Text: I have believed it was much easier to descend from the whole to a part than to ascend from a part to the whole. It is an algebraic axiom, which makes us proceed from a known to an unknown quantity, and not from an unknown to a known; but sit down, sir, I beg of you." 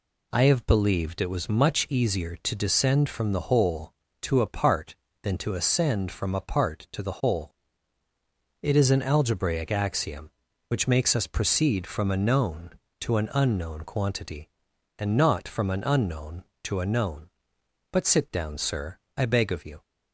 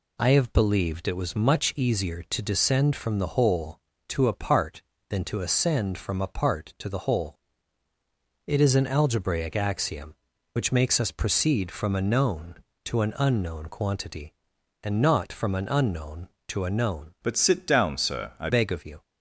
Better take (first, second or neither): first